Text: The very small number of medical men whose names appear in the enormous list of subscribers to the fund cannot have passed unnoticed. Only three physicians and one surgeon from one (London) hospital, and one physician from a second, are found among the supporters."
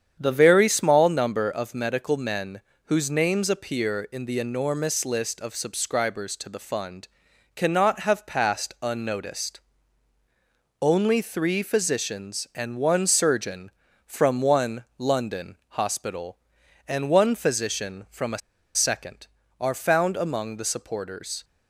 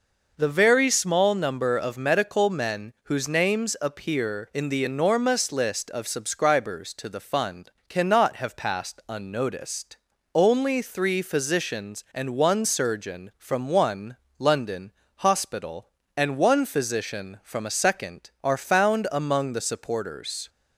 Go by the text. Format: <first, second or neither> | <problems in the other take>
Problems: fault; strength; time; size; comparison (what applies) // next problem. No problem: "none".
second | starts louder than the rest; strong; until 1.2 s; 8 dB // pauses between "men" and "whose"; slight; at 2.6 s; 0.24 s long // pauses between "fund" and "cannot"; noticeable; at 7.0 s; 0.48 s long; slight in the second // pauses between "a" and "second"; at 18.4 s; 0.37 s long